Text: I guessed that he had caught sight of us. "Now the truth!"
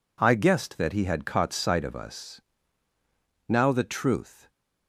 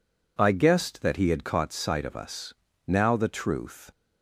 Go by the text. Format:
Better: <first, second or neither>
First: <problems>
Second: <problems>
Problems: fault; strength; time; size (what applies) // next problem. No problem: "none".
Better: neither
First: none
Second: none